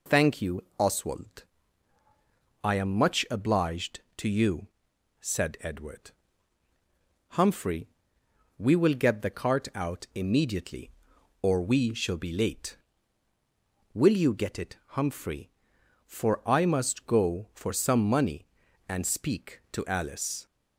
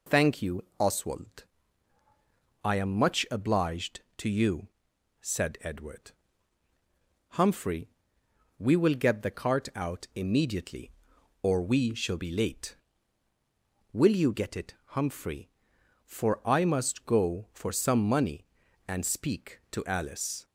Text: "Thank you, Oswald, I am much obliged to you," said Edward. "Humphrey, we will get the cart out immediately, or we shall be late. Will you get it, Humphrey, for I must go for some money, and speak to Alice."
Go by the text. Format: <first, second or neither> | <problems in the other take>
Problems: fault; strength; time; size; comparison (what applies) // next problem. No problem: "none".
neither | none